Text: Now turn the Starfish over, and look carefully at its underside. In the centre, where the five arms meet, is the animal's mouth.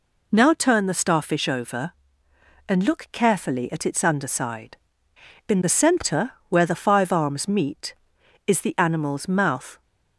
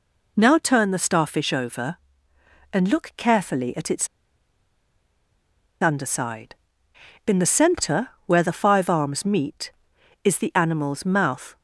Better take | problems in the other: first | pauses between "its" and "underside"; strong; at 4.0 s; 1.7 s long

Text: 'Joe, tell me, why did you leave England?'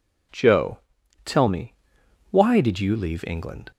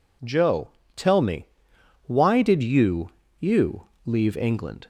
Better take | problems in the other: first | says "you" twice; at 3.3 s

